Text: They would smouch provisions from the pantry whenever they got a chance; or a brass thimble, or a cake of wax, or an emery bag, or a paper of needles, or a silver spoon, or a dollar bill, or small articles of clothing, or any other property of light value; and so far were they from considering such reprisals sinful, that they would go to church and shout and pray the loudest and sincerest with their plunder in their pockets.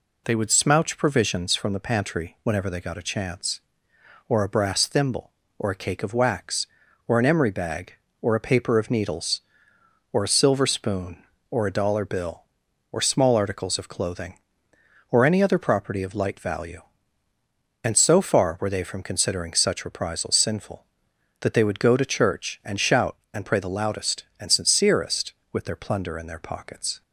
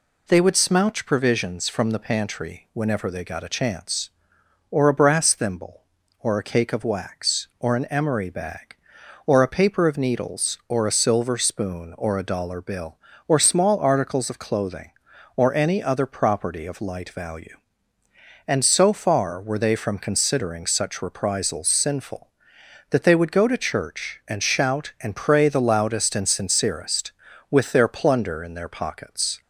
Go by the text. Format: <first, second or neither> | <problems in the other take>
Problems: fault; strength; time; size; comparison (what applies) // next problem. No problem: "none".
neither | none